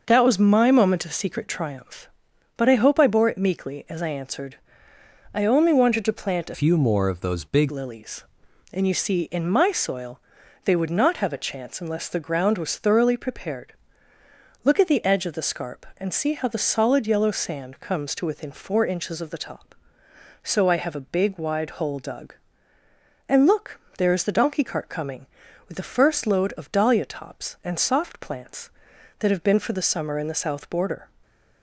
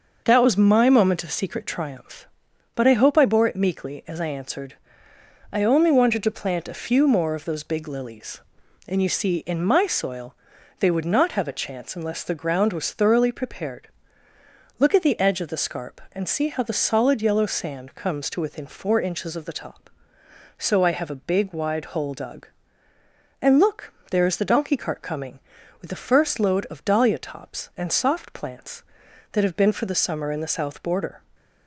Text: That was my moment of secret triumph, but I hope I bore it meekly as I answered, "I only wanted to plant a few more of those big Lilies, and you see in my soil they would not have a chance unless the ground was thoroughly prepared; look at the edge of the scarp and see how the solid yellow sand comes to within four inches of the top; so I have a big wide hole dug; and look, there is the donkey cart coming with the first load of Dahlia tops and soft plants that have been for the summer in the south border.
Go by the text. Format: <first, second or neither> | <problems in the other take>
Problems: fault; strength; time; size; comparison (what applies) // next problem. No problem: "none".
second | starts louder than the rest; noticeable; until 1.0 s; 6 dB; noticeable in the second // changes voice from "few" to "big"; from 6.5 to 7.6 s; 1.1 s long // pauses between "soil" and "they"; noticeable; at 10.1 s; 0.46 s long; noticeable in the second